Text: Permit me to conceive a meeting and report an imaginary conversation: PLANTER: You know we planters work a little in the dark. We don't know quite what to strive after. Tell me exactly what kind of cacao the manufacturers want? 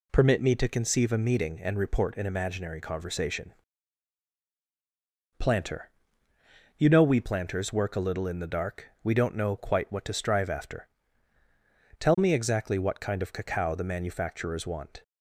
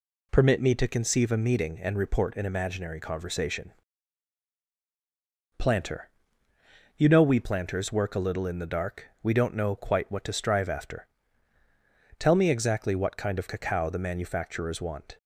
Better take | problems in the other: neither | none

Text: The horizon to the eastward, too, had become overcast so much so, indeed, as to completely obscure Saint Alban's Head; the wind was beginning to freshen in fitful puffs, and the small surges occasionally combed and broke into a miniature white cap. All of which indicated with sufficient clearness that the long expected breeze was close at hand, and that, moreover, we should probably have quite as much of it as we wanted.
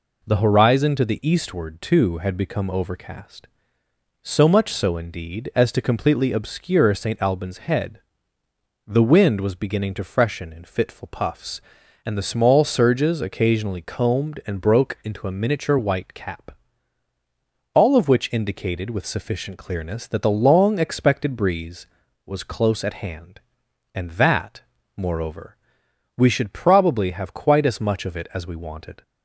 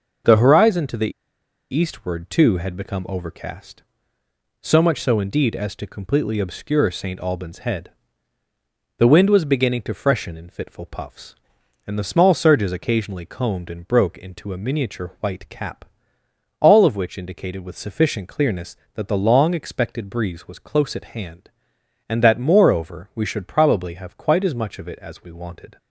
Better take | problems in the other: first | pauses between "the" and "eastward"; noticeable; at 1.1 s; 0.61 s long

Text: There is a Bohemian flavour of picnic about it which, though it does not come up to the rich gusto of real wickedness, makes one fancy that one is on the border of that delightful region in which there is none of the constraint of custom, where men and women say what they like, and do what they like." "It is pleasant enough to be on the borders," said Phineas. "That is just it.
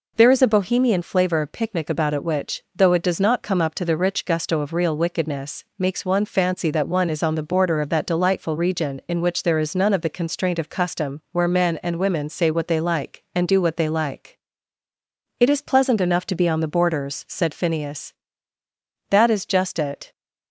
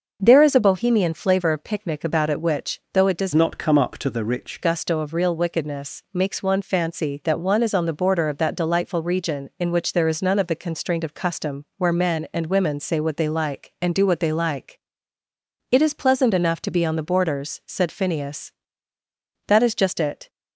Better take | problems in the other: first | starts louder than the rest; noticeable; until 1.2 s; 6 dB // changes voice from "not" to "rich"; from 3.3 to 4.5 s; 1.2 s long

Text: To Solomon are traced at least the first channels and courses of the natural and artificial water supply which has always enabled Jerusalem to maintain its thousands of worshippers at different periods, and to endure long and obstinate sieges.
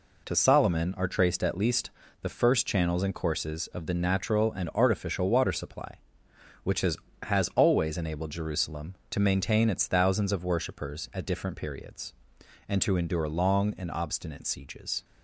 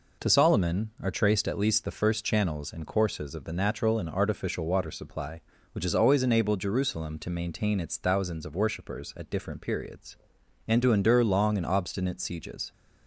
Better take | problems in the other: second | pauses between "least" and "the"; slight; at 1.9 s; 0.32 s long // says "has" twice; at 7.2 s

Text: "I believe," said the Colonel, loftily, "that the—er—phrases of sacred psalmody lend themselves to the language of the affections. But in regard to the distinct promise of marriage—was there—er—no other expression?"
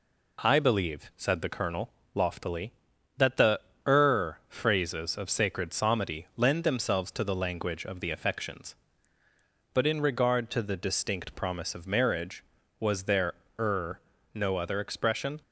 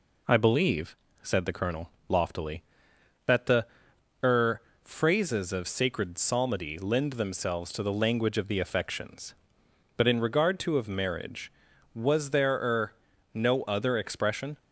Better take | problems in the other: first | skips "the distinct promise"; at 10.7 s

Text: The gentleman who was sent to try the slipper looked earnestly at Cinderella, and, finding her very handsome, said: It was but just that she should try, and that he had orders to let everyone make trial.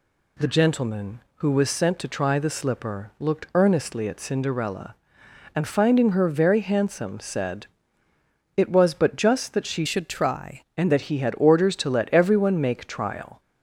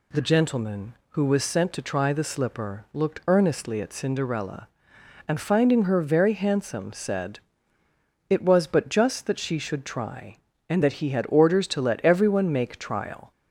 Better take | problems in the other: second | changes voice from "should" to "try"; from 9.8 to 10.5 s; 0.7 s long

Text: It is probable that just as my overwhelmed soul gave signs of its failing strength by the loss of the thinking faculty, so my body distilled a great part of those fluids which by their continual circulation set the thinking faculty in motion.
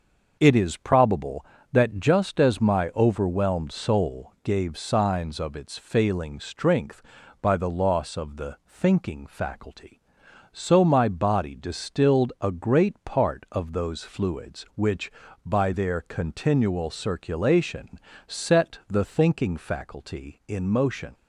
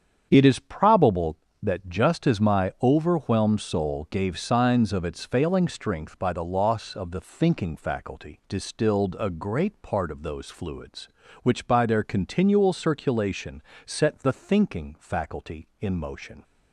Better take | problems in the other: first | starts louder than the rest; strong; until 1.3 s; 8.5 dB; also in the first // skips "so my body"; at 8.4 s // pauses between "circulation" and "set"; slight; at 13.6 s; 0.24 s long; slight in the first

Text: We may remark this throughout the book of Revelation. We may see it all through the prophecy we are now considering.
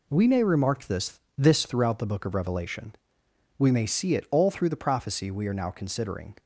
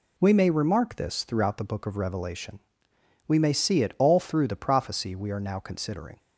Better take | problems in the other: second | says "this" twice; at 1.3 s

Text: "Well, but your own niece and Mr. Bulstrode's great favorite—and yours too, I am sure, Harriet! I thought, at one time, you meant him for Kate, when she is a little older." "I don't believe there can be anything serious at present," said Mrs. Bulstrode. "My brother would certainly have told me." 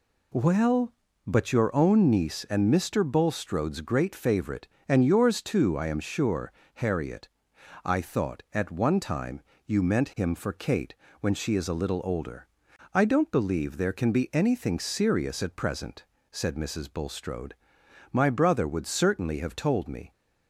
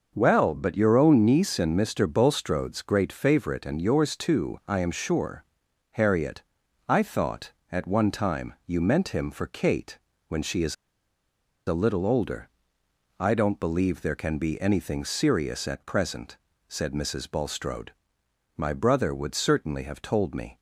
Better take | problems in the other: first | starts louder than the rest; until 1.1 s; 6 dB // pauses between "is" and "a"; noticeable; at 10.7 s; 0.92 s long

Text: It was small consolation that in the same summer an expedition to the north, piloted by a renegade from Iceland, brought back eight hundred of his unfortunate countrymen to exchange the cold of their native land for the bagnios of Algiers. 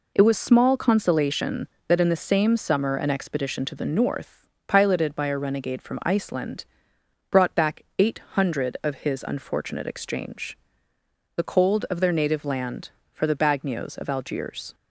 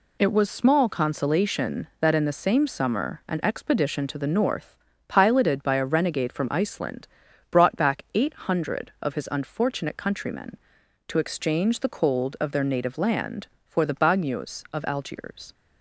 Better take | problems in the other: second | pauses between "back" and "eight"; slight; at 7.8 s; 0.16 s long // skips "countrymen to"; at 9.8 s // pauses between "exchange" and "the"; noticeable; at 10.5 s; 0.80 s long

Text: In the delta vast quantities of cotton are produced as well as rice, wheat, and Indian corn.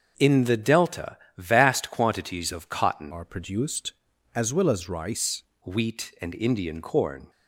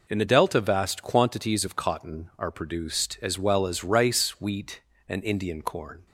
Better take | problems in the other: second | starts louder than the rest; until 1.1 s; 6.5 dB // pauses between "delta" and "vast"; slight; at 1.1 s; 0.20 s long // changes voice from "are" to "rice"; from 3.1 to 5.4 s; 2.3 s long

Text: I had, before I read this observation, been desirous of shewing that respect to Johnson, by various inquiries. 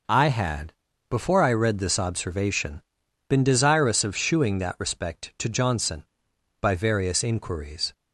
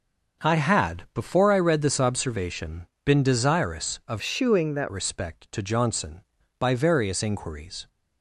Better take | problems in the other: first | starts louder than the rest; until 1.5 s; 6.5 dB // changes voice from "shewing" to "that"; from 4.2 to 4.8 s; 0.6 s long

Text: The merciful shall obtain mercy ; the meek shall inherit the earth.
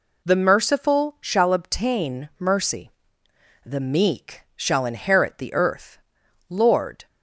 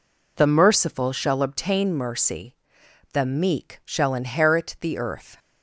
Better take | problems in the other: second | goes on to say "Lord"; from 6.4 s on; 0.58 s long

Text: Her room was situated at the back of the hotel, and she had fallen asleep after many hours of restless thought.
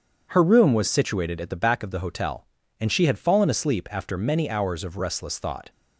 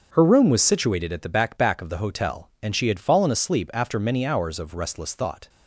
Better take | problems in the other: first | starts louder than the rest; until 1.1 s; 6.5 dB; strong in the first // says "back" twice; at 1.5 s

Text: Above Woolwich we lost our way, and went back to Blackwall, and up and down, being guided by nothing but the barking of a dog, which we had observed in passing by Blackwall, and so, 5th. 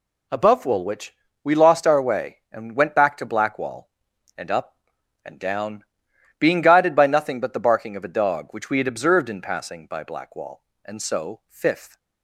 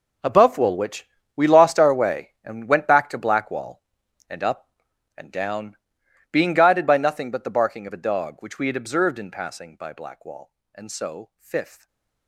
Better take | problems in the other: first | gets quieter; strong; throughout; 15 dB // pauses between "Woolwich" and "we"; slight; at 1.0 s; 0.28 s long; slight in the first // stays silent after the last word; slight; from 11.7 s on; 0.5 s long

